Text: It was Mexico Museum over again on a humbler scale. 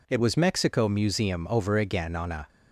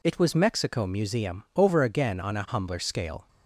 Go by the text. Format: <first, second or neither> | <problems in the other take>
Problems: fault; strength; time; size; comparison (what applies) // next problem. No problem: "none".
second | stops before "humbler scale"; at 2.4 s